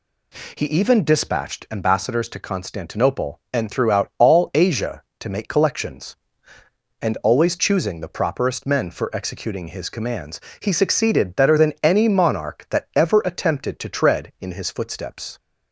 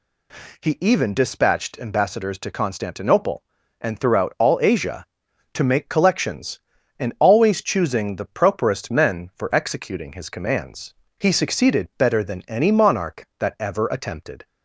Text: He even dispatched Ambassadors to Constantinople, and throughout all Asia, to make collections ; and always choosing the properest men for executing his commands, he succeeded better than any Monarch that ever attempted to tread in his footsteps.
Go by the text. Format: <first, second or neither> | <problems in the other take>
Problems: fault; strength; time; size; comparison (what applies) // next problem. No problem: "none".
first | stops before "to tread in his footsteps"; at 14.4 s